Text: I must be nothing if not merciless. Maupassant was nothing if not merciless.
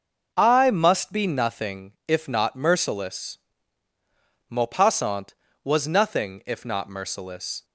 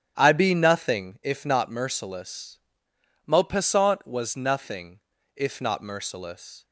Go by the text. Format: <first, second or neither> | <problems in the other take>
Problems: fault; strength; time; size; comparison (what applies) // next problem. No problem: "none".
first | starts louder than the rest; strong; until 1.1 s; 10 dB // skips "must"; at 0.3 s // pauses between "nothing" and "if"; at 4.9 s; 0.38 s long